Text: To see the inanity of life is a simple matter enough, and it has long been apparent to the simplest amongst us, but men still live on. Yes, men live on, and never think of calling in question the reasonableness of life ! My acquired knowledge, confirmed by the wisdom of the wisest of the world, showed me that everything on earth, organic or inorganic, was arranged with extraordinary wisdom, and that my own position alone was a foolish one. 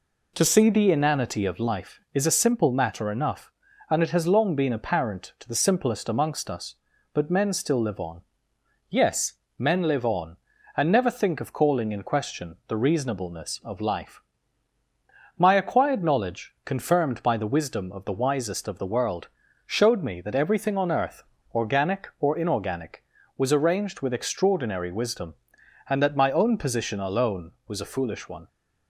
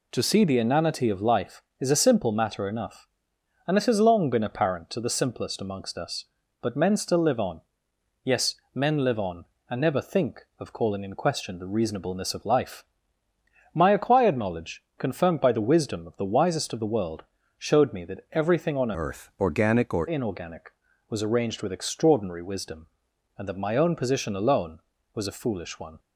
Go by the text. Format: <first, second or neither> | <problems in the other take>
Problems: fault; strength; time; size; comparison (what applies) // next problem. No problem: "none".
first | changes voice from "earth" to "or"; from 18.9 to 20.0 s; 1.1 s long